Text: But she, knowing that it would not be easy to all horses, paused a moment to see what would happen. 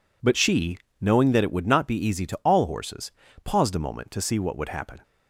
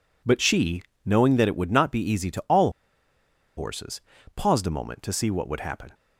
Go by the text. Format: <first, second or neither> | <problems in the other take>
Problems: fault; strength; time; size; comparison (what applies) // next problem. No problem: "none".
first | pauses between "all" and "horses"; noticeable; at 2.7 s; 0.86 s long